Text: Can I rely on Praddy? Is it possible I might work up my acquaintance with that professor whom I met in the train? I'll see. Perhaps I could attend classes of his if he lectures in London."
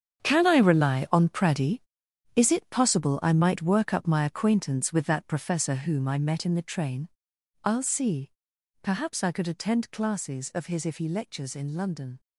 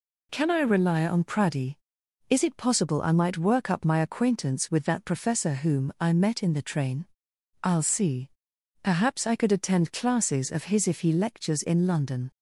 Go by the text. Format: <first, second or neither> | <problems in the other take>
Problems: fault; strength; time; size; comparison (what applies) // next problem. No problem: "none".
second | gets quieter; strong; throughout; 12 dB